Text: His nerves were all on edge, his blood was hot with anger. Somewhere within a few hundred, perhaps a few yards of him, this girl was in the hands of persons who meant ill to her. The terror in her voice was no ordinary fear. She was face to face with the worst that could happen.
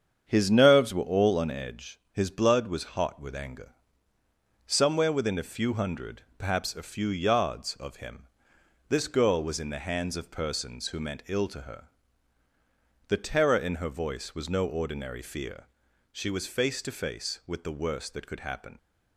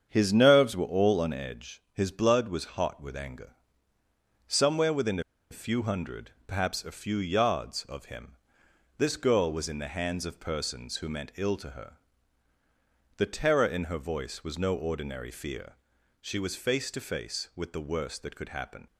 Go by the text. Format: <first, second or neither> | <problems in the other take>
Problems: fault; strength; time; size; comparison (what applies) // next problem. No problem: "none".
first | starts louder than the rest; strong; until 1.1 s; 7.5 dB; strong in the first // pauses between "within" and "a"; slight; at 5.1 s; 0.30 s long